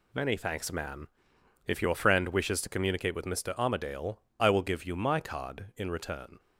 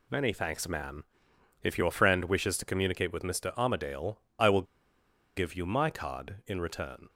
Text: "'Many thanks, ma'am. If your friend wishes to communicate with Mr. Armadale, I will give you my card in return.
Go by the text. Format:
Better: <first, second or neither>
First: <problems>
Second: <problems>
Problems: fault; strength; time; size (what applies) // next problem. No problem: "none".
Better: first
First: none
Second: pauses between "will" and "give"; noticeable; at 4.6 s; 0.73 s long